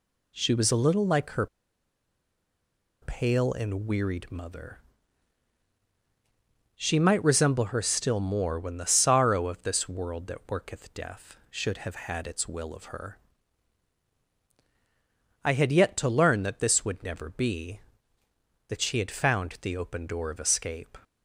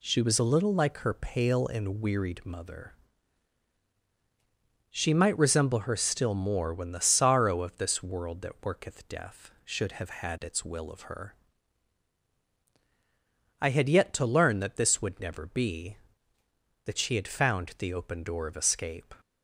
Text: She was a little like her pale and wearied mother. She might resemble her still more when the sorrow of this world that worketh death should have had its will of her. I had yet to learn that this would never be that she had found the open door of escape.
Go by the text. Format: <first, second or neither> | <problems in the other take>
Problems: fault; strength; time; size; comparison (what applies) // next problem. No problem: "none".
second | pauses between "her" and "pale"; strong; at 1.4 s; 1.5 s long